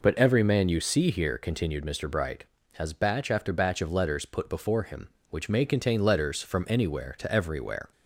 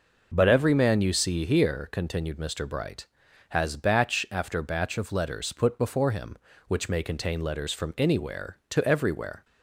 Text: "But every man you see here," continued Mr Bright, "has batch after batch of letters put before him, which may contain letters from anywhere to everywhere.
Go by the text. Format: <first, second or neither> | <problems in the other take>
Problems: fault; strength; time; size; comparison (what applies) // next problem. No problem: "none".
neither | none